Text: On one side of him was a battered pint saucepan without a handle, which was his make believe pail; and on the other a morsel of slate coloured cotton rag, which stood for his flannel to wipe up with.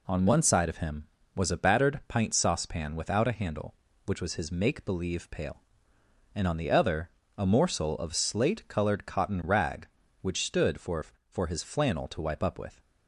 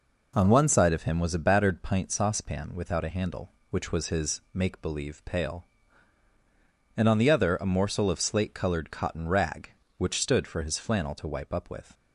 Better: second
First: pauses between "other" and "a"; slight; at 7.0 s; 0.30 s long // says "for" twice; at 11.3 s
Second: none

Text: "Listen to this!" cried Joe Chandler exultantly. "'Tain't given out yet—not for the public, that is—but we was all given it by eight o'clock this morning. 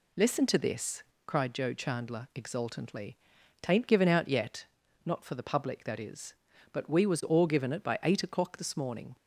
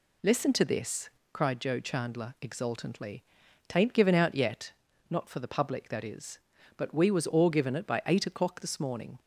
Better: neither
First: none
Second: none

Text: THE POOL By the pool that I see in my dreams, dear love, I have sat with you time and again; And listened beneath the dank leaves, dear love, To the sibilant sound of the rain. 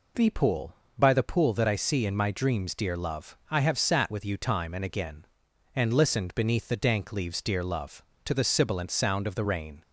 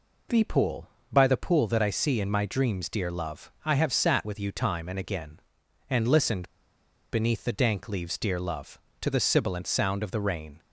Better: first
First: none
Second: pauses between "listened" and "beneath"; noticeable; at 6.4 s; 0.63 s long

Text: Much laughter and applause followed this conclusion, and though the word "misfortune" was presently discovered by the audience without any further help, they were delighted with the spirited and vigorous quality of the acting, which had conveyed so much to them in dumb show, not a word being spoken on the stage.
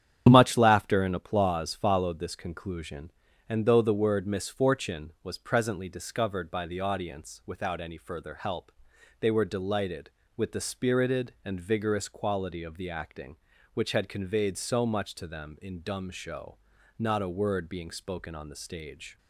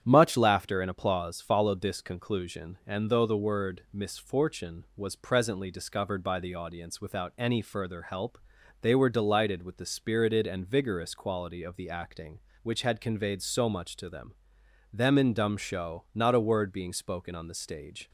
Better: first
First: starts louder than the rest; strong; until 1.3 s; 9 dB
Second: starts louder than the rest; strong; until 1.0 s; 9.5 dB // says "them" twice; at 14.9 s

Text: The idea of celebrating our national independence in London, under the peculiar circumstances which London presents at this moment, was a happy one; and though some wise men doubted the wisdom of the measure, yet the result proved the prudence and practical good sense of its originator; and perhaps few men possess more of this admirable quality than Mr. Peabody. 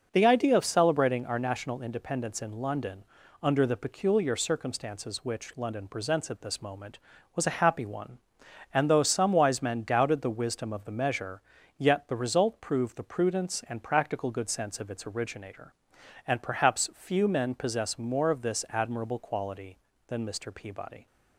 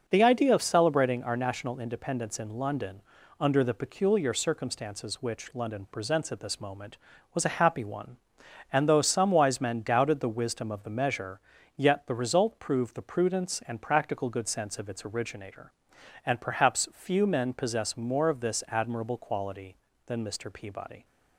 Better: neither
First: none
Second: none

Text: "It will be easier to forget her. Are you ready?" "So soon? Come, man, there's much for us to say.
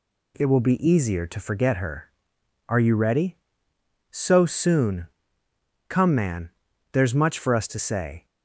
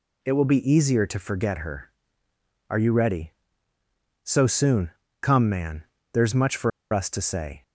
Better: first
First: none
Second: pauses between "for" and "us"; slight; at 6.7 s; 0.22 s long

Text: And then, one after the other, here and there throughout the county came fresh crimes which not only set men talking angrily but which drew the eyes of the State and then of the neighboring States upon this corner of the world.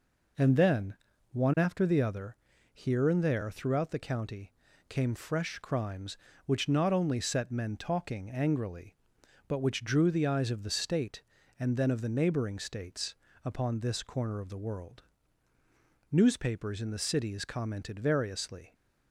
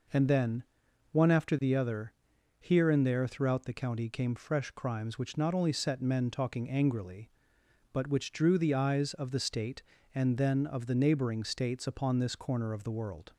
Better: second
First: pauses between "county" and "came"; slight; at 4.5 s; 0.36 s long // pauses between "States" and "upon"; slight; at 13.1 s; 0.28 s long // goes on to say "Newspapers in the cities commented variously"; strong; from 16.1 s on; 2.6 s long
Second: none

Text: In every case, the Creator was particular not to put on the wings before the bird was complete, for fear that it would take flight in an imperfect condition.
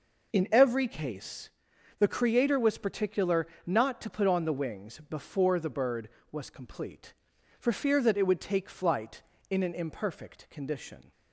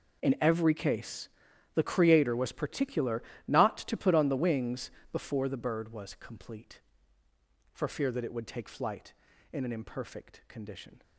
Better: first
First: pauses between "particular" and "not"; slight; at 3.4 s; 0.20 s long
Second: gets quieter; strong; throughout; 16 dB // pauses between "particular" and "not"; slight; at 3.2 s; 0.24 s long // pauses between "wings" and "before"; slight; at 4.9 s; 0.22 s long

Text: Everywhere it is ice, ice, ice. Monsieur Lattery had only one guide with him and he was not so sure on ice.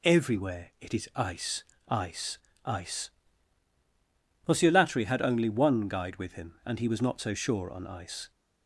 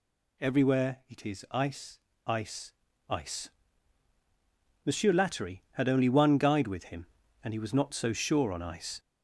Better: first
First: none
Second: gets louder; throughout; 3.5 dB

